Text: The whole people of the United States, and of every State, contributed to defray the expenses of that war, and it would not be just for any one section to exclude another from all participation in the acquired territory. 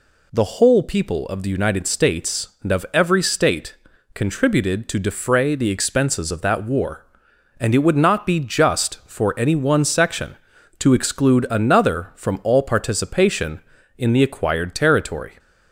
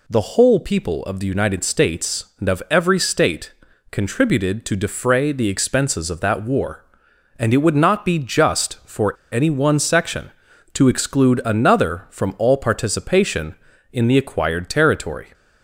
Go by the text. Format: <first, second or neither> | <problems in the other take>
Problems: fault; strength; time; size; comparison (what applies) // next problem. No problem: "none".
first | pauses between "for" and "any"; slight; at 9.1 s; 0.17 s long